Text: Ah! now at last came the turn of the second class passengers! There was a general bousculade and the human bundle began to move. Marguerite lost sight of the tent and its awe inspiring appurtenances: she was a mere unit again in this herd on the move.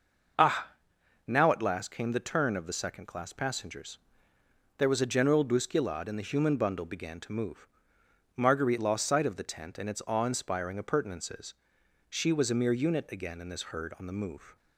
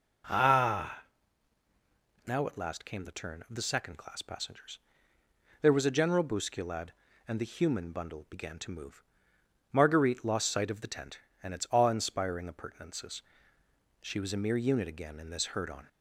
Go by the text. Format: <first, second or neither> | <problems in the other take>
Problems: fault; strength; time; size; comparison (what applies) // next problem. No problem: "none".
first | stops before "the move"; at 15.8 s